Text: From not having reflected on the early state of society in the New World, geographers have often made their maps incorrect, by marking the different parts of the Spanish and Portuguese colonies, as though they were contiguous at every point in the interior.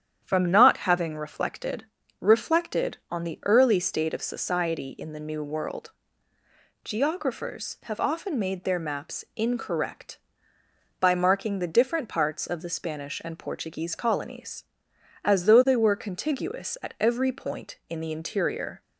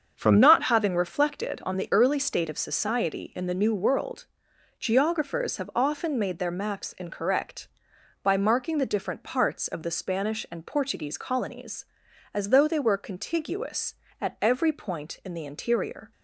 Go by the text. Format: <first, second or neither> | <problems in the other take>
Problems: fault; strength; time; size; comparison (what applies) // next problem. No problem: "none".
second | starts louder than the rest; strong; until 1.2 s; 9.5 dB; also in the second // says "reflected" twice; at 2.2 s